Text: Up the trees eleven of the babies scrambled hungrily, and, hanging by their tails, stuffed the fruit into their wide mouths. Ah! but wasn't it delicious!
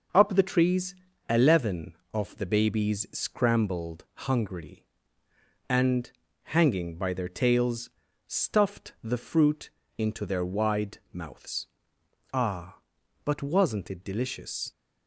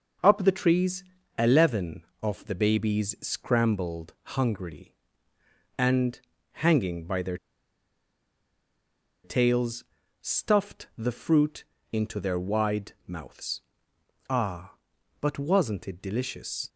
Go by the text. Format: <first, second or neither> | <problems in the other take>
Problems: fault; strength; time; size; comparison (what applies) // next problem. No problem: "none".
first | pauses between "trees" and "eleven"; slight; at 1.0 s; 0.32 s long; slight in the first // pauses between "scrambled" and "hungrily"; slight; at 4.1 s; 0.20 s long; slight in the first // pauses between "their" and "tails"; strong; at 7.3 s; 1.8 s long // pauses between "fruit" and "into"; slight; at 11.6 s; 0.28 s long; slight in the first